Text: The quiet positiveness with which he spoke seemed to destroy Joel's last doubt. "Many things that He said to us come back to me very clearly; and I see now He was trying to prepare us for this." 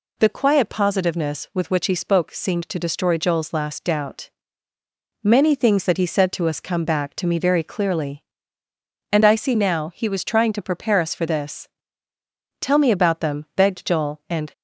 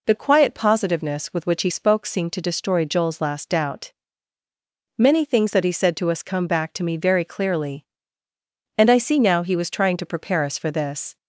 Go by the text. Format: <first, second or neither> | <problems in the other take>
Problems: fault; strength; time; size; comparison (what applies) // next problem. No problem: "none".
second | goes on to say "Tell me about them begged Joel and"; strong; from 12.6 s on; 1.9 s long